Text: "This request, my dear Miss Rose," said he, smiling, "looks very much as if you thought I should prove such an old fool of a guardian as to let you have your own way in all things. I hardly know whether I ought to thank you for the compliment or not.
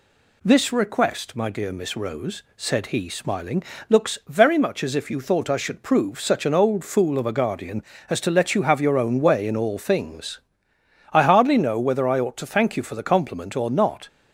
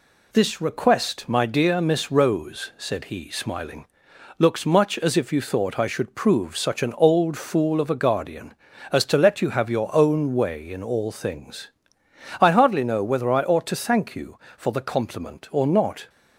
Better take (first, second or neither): first